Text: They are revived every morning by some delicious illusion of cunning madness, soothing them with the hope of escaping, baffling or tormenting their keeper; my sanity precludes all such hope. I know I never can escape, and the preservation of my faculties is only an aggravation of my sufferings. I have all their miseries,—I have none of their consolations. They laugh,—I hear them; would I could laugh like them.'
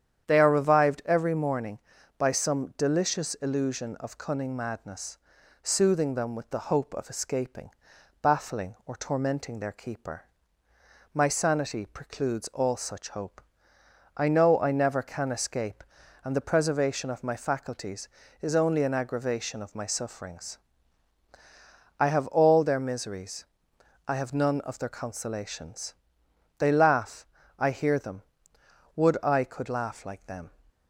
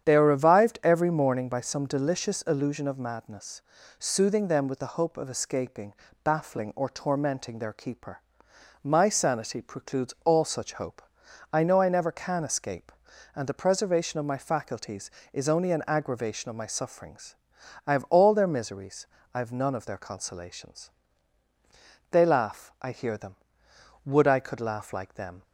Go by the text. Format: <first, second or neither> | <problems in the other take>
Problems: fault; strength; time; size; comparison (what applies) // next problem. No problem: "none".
first | starts louder than the rest; strong; until 1.0 s; 8.5 dB; strong in the first // skips "cunning"; at 2.9 s